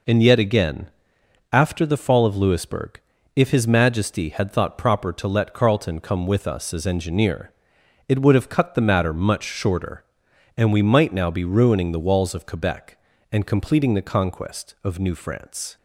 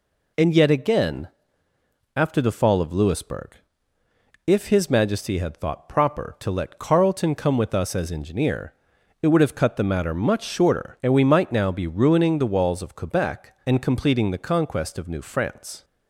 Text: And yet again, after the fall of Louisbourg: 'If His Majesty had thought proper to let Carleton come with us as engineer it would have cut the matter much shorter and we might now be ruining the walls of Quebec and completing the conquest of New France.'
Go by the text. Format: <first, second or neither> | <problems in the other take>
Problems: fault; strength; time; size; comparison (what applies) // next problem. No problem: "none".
neither | pauses between "engineer" and "it"; noticeable; the same in both